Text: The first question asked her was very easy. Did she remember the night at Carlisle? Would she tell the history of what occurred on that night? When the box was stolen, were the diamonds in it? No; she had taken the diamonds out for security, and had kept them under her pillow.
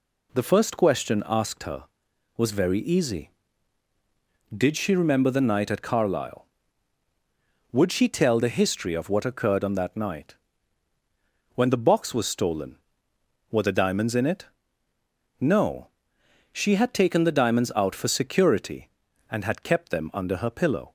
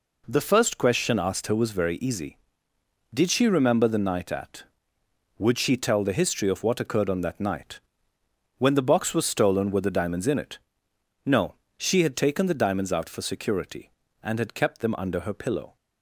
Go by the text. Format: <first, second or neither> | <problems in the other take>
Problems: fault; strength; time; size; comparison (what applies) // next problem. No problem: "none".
first | skips "Carlisle"; at 4.9 s